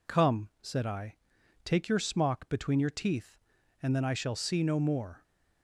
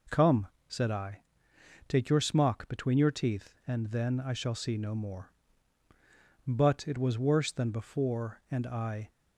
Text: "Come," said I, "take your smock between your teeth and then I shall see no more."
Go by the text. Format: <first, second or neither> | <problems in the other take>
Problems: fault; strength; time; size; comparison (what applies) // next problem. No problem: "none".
first | goes on to say "But it was worse than before and I"; strong; from 6.4 s on; 2.6 s long